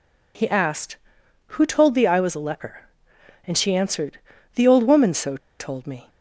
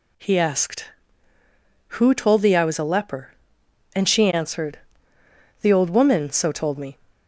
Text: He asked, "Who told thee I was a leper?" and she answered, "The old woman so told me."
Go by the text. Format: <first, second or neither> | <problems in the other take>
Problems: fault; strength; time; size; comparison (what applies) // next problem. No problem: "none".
second | pauses between "so" and "told"; slight; at 5.3 s; 0.20 s long